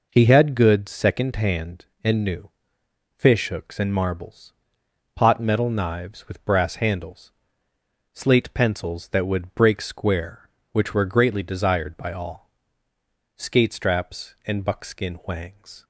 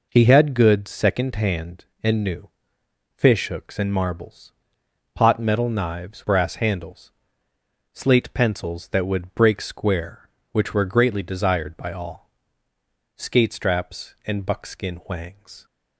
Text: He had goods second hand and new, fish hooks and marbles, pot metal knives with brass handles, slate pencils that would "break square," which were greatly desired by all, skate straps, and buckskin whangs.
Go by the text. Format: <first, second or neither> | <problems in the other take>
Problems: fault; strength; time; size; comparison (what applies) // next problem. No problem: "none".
first | skips "with"; at 6.2 s